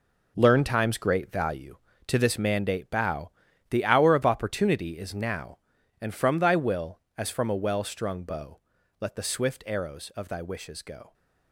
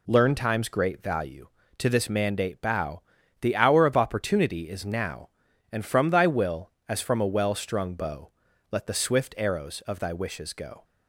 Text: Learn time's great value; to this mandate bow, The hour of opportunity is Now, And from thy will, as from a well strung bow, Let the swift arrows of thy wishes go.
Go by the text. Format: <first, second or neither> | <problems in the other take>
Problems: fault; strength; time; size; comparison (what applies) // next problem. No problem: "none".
second | gets quieter; strong; throughout; 10.5 dB